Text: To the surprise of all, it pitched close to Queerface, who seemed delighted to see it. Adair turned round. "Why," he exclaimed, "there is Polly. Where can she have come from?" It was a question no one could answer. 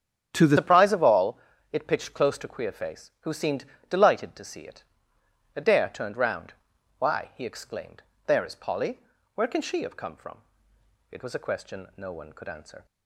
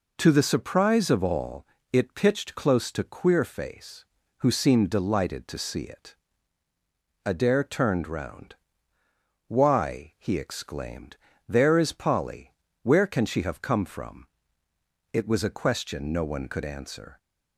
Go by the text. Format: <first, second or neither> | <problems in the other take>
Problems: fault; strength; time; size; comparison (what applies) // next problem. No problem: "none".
second | starts louder than the rest; strong; until 1.3 s; 8.5 dB // changes voice at "surprise"; from 0.5 s on; 12.3 s long // pauses between "seemed" and "delighted"; slight; at 3.6 s; 0.24 s long